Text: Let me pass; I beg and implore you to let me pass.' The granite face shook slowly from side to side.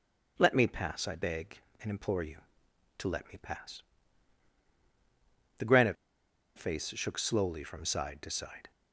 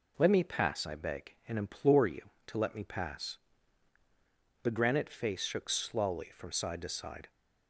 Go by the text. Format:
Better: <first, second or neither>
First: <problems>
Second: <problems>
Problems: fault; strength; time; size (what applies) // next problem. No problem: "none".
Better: second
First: starts louder than the rest; until 1.3 s; 7 dB // pauses between "granite" and "face"; noticeable; at 5.9 s; 0.62 s long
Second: none